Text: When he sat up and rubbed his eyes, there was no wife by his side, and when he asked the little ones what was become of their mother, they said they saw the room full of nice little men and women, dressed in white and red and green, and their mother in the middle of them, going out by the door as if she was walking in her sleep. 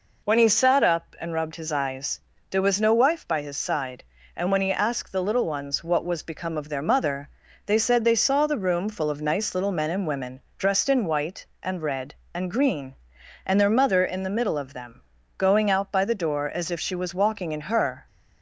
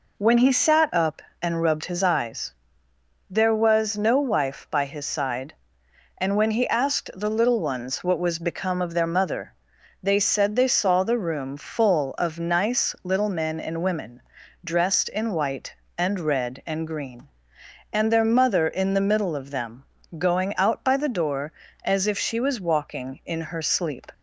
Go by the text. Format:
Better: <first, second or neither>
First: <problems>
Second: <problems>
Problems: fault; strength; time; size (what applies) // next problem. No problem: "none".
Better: second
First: stops before "sleep"; at 18.0 s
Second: none